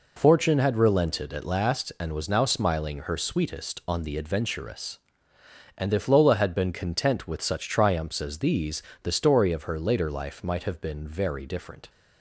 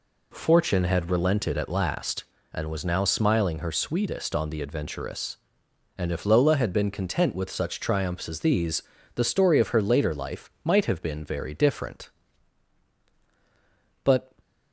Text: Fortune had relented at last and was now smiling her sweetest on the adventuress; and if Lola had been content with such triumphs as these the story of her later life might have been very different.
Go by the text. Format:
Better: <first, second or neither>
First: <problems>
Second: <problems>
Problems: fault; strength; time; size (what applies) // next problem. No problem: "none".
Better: first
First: pauses between "these" and "the"; slight; at 8.8 s; 0.22 s long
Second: pauses between "these" and "the"; slight; at 8.8 s; 0.32 s long // goes on to say "But"; slight; from 14.0 s on; 0.28 s long